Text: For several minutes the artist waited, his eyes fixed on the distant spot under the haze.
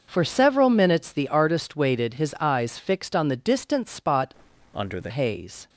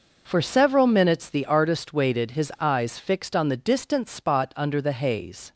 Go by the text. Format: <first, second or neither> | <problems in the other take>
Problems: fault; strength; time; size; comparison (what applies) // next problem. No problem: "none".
second | starts louder than the rest; noticeable; until 1.0 s; 6 dB // changes voice from "under" to "the"; from 4.7 to 5.1 s; 0.4 s long